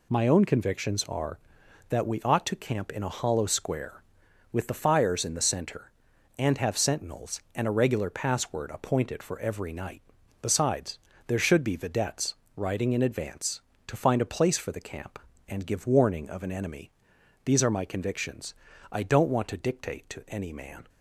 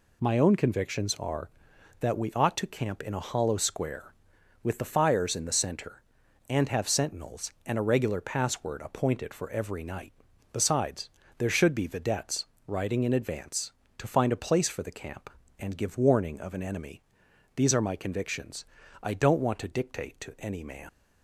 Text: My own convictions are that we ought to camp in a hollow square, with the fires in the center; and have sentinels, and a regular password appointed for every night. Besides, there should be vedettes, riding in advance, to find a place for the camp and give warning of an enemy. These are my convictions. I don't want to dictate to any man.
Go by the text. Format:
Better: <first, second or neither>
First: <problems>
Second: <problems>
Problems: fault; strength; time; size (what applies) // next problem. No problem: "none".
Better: first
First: none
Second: leaves "man" unfinished; at 20.8 s; 100 ms